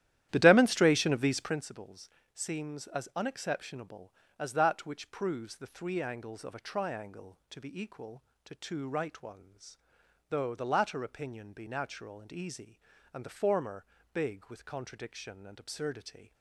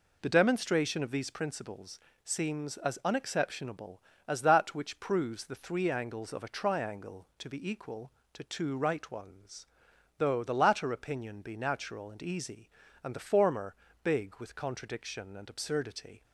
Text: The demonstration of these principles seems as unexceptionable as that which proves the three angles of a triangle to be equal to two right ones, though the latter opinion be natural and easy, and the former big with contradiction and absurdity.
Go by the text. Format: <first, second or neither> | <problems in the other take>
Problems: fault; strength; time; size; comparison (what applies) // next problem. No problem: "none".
second | starts louder than the rest; strong; until 1.7 s; 12.5 dB // pauses between "principles" and "seems"; slight; at 2.0 s; 0.26 s long; slight in the second // pauses between "former" and "big"; slight; at 13.8 s; 0.26 s long; slight in the second